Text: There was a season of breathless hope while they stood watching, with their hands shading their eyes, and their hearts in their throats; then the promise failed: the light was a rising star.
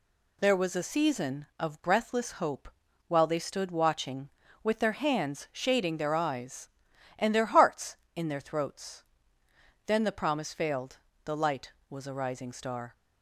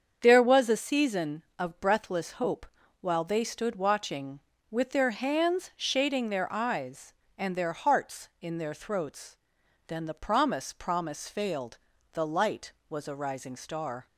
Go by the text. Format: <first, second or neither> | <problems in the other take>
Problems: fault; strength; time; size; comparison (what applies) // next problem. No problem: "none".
first | starts louder than the rest; strong; until 1.2 s; 7.5 dB // pauses between "hope" and "while"; slight; at 2.6 s; 0.36 s long; also in the first // says "promise" twice; at 10.7 s